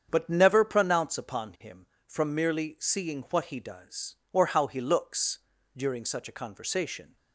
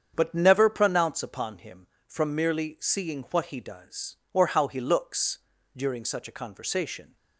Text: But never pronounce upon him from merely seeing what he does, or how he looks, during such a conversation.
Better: neither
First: starts louder than the rest; strong; until 1.1 s; 7.5 dB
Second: starts louder than the rest; strong; until 1.1 s; 7.5 dB

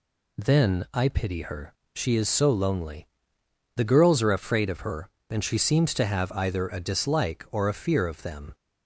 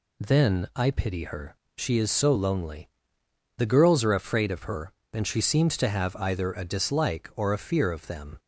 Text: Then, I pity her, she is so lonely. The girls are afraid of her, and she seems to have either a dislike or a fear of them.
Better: neither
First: none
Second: none

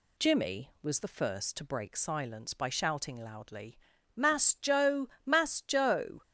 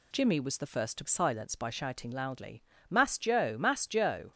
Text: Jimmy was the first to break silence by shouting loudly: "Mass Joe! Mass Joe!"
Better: first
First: none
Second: skips "break"; at 1.0 s

